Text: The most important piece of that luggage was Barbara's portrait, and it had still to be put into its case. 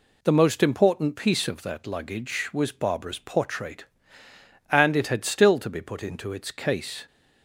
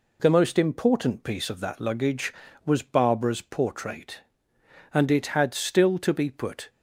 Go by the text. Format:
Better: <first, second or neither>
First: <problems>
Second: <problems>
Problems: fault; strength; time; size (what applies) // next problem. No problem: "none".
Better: first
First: none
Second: stops before "into its case"; at 6.6 s